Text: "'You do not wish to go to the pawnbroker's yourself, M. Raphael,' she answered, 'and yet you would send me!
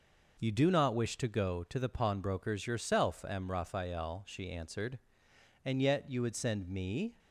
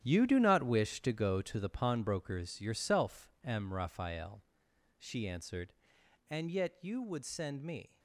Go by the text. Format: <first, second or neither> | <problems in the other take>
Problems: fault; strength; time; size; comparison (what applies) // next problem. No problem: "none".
first | gets quieter; strong; throughout; 12.5 dB